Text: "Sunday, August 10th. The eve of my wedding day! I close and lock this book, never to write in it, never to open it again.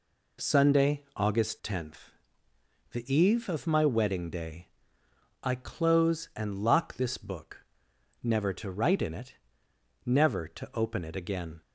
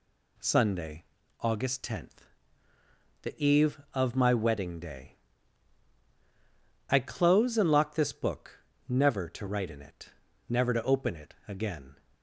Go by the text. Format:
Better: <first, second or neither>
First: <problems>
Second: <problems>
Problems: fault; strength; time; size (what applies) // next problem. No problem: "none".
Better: neither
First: none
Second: none